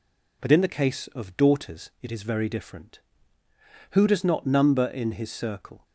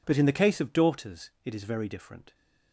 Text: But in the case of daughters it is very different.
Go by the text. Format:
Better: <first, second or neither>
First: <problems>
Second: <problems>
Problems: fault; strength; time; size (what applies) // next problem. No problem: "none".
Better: second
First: goes on to say "Who does not number in his circle"; strong; from 3.9 s on; 1.9 s long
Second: none